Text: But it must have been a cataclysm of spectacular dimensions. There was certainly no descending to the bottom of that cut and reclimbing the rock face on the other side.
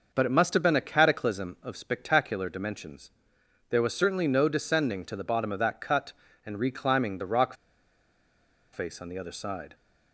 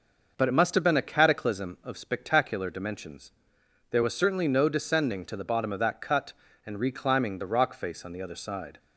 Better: second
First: pauses between "rock" and "face"; at 7.5 s; 1.1 s long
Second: none

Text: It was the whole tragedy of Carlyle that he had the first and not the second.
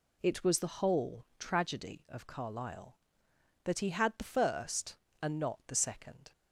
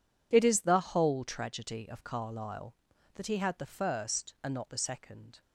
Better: first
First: none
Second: says "is" for "was"; at 0.4 s

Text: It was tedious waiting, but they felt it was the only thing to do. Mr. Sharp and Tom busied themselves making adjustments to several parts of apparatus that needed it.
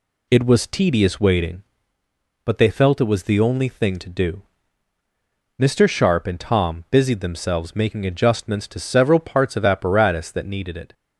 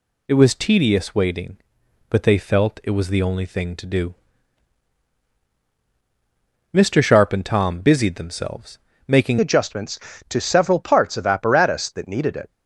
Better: first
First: none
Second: pauses between "themselves" and "making"; slight; at 8.7 s; 0.30 s long // changes voice at "adjustments"; from 9.3 s on; 3.2 s long

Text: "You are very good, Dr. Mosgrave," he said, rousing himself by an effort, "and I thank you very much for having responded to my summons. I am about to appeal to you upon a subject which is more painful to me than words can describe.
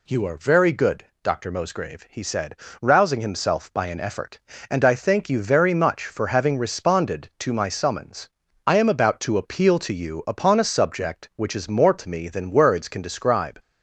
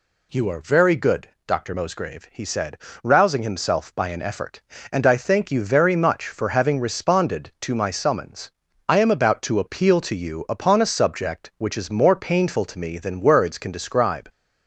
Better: second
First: skips "painful"; at 11.9 s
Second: none

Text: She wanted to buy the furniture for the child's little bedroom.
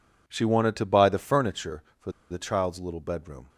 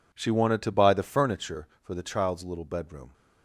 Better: second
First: pauses between "for" and "the"; slight; at 2.0 s; 0.20 s long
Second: none

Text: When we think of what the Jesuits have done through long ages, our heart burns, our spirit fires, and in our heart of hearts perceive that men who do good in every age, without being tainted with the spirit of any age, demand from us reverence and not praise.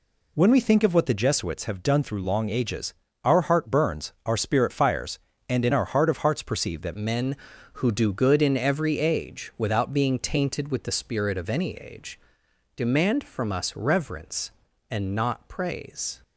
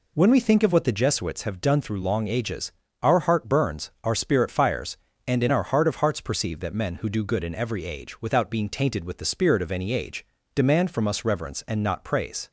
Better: second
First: changes voice at "men"; from 6.9 s on; 9.3 s long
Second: none

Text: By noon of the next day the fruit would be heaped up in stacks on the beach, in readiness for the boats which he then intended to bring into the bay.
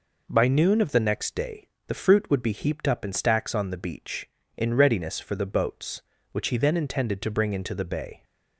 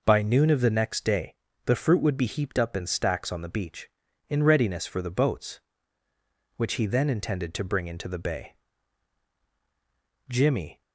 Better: first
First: pauses between "day" and "the"; slight; at 1.6 s; 0.20 s long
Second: pauses between "day" and "the"; slight; at 1.3 s; 0.30 s long // goes on to say "Jimmy"; from 10.2 s on; 0.54 s long

